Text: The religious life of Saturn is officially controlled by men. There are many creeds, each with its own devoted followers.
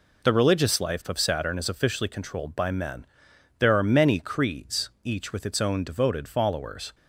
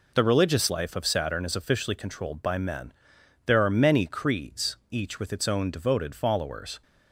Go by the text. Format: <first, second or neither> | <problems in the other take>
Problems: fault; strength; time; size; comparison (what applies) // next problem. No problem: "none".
neither | none